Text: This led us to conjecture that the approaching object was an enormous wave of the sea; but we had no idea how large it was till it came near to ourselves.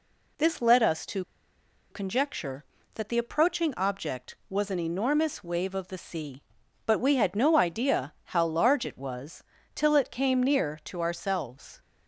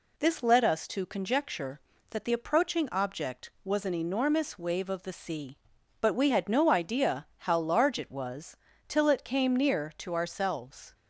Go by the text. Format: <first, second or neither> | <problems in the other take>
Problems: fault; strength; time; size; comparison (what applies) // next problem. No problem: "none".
second | pauses between "to" and "conjecture"; noticeable; at 1.2 s; 0.67 s long // pauses between "was" and "till"; slight; at 9.4 s; 0.32 s long; slight in the second